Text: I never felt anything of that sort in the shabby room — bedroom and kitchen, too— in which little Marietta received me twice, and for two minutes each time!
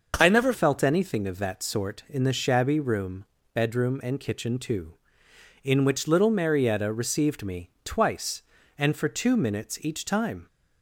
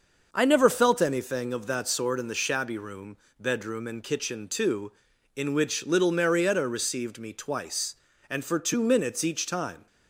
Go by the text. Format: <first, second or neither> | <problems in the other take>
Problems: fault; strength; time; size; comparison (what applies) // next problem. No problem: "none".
second | starts louder than the rest; until 1.1 s; 6 dB; also in the second // changes voice at "felt"; from 0.5 s on; 9.9 s long // pauses between "me" and "twice"; slight; at 7.6 s; 0.16 s long